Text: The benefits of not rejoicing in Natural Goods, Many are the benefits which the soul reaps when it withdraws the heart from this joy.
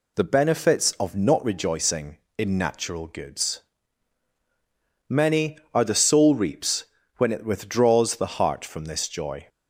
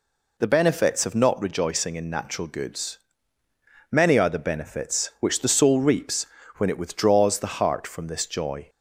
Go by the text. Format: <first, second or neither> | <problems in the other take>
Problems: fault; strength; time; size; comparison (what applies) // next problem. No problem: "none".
second | skips "benefits which the"; at 5.9 s // pauses between "reaps" and "when"; slight; at 6.8 s; 0.32 s long; slight in the second